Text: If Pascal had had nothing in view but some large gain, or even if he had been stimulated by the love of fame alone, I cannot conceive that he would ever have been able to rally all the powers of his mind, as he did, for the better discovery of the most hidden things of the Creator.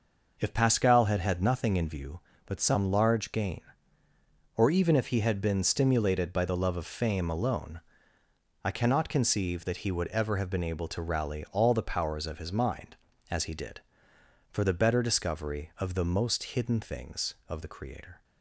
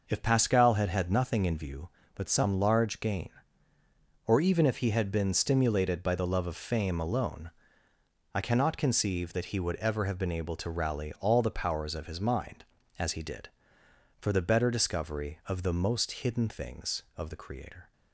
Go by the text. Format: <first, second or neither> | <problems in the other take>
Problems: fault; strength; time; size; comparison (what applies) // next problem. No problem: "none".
neither | none